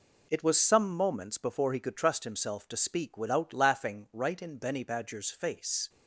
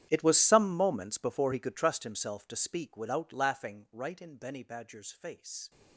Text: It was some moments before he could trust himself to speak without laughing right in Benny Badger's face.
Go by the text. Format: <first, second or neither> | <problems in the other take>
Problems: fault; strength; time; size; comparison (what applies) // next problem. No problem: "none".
first | gets quieter; strong; throughout; 19 dB